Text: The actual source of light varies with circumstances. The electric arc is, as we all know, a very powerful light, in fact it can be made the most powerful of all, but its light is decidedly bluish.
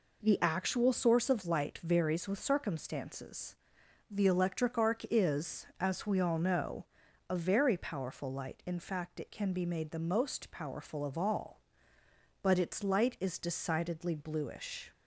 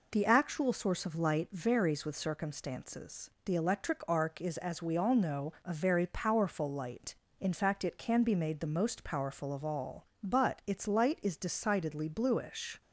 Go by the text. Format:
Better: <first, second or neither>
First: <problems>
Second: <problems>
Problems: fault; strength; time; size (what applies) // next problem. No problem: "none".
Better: neither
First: none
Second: none